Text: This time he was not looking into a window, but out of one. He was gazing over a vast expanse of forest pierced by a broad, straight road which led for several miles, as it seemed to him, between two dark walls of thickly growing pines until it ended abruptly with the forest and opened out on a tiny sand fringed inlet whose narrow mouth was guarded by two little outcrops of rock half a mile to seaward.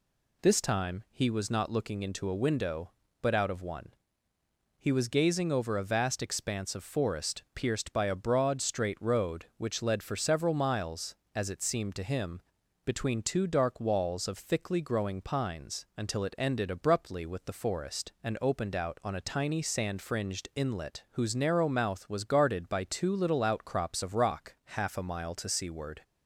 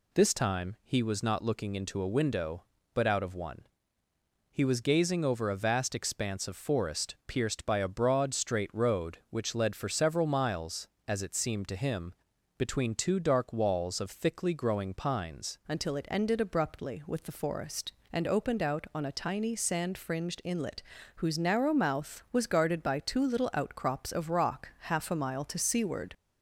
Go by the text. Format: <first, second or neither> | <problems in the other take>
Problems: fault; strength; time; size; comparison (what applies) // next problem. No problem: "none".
first | changes voice at "until"; from 15.6 s on; 10.5 s long // pauses between "inlet" and "whose"; slight; at 20.8 s; 0.32 s long